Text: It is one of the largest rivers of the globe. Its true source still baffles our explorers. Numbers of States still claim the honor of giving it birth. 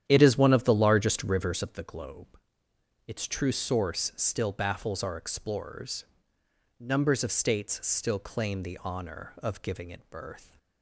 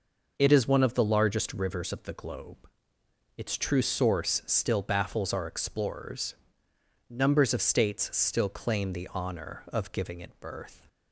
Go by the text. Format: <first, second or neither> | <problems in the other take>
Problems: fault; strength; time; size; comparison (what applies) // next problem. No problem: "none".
second | starts louder than the rest; strong; until 1.9 s; 10 dB